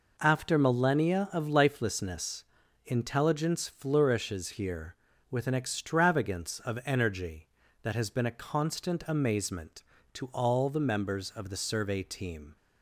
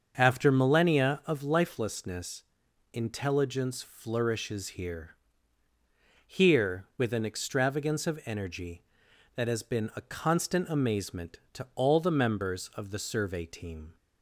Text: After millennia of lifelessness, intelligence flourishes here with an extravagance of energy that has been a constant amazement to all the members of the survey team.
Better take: first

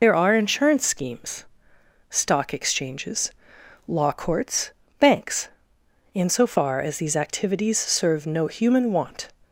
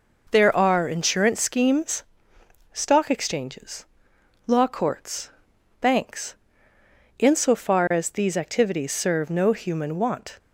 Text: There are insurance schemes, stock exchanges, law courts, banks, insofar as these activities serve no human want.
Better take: second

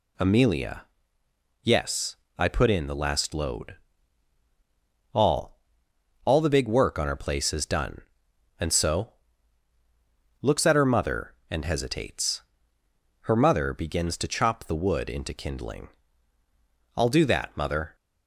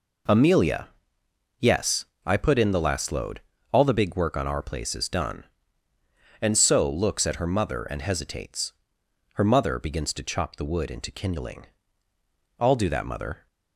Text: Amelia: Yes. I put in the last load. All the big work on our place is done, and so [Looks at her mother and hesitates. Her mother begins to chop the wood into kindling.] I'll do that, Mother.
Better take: second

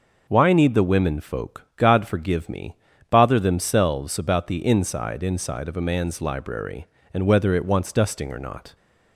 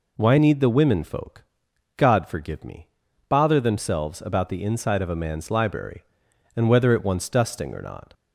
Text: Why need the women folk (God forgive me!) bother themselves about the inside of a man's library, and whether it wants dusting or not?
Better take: second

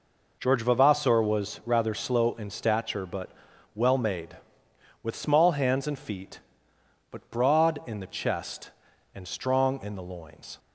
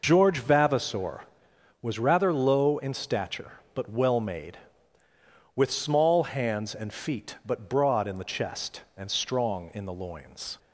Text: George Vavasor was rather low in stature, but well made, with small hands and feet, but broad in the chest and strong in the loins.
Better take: second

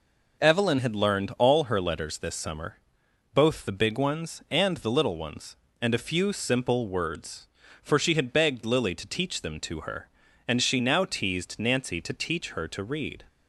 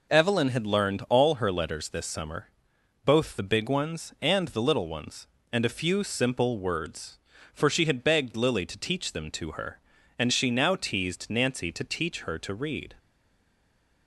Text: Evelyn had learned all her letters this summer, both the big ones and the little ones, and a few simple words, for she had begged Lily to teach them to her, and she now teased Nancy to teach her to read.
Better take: first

